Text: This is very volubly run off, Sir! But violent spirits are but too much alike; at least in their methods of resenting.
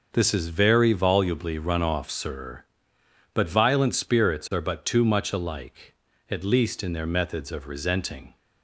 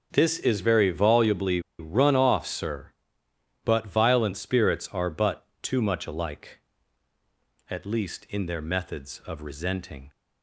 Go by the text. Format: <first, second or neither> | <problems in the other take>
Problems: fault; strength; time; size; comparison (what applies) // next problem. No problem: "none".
first | pauses between "volubly" and "run"; slight; at 1.6 s; 0.17 s long // pauses between "but" and "too"; slight; at 5.4 s; 0.16 s long